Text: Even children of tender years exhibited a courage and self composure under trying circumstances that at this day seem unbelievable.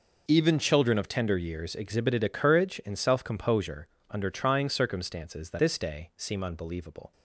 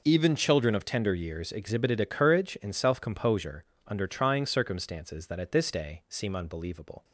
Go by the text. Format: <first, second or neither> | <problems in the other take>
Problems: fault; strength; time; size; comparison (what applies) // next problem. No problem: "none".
second | pauses between "composure" and "under"; slight; at 3.8 s; 0.24 s long; slight in the second // skips "at"; at 5.5 s